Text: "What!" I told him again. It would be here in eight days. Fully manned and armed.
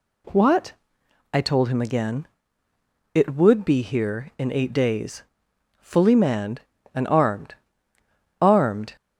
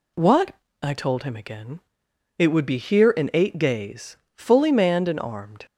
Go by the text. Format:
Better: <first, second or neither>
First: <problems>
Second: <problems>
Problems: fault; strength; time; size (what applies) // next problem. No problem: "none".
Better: second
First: says "armed" twice; at 8.4 s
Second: none